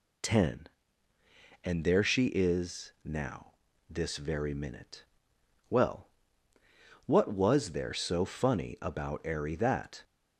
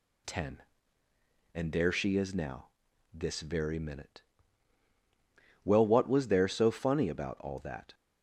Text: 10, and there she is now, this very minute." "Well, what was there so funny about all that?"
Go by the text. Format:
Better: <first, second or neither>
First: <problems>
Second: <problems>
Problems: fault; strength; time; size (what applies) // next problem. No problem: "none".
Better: second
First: says "airy" for "all"; at 9.2 s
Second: none